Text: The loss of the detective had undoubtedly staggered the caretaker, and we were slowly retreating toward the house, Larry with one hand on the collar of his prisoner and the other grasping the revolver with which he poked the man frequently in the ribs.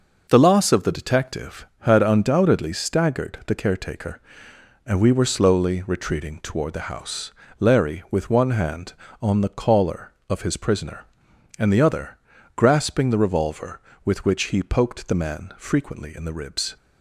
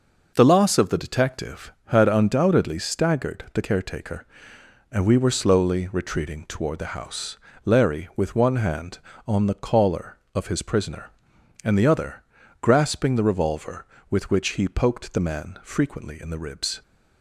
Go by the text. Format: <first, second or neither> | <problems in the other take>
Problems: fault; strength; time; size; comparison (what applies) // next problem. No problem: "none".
neither | pauses between "other" and "grasping"; the same in both